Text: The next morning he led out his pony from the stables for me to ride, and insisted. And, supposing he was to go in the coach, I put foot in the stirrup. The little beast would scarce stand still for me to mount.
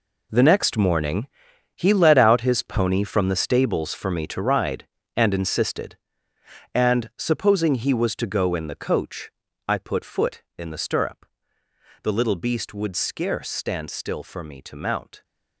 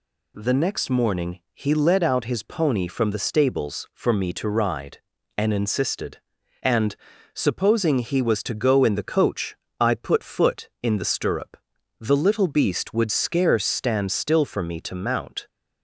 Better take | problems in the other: second | gets quieter; strong; throughout; 13 dB // pauses between "morning" and "he"; noticeable; at 1.2 s; 0.48 s long

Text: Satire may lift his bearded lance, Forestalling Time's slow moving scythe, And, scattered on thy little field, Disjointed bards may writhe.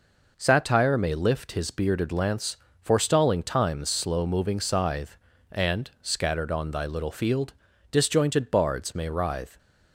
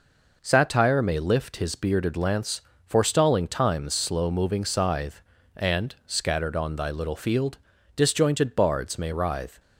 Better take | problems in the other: neither | none

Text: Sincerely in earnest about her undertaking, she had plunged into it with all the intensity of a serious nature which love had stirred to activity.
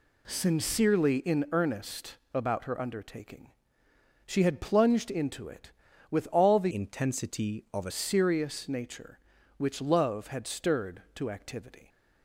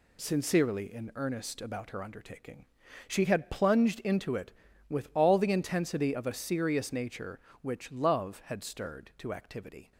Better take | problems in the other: second | pauses between "earnest" and "about"; slight; at 2.1 s; 0.18 s long // changes voice from "intensity" to "a"; from 6.7 to 7.9 s; 1.2 s long

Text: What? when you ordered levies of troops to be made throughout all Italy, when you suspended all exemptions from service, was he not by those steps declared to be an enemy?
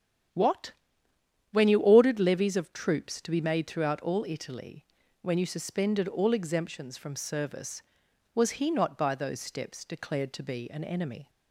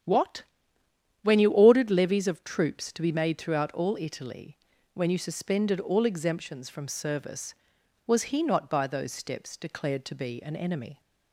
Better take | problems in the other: neither | starts louder than the rest; strong; the same in both

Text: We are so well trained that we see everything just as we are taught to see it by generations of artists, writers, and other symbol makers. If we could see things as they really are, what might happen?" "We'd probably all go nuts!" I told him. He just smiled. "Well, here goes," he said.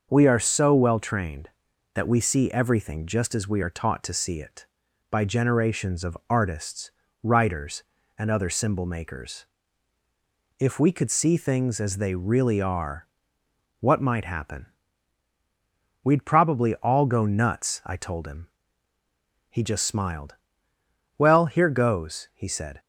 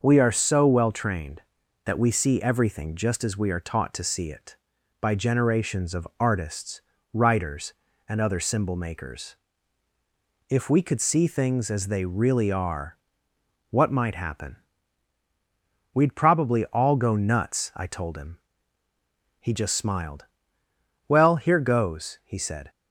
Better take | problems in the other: neither | starts louder than the rest; noticeable; the same in both

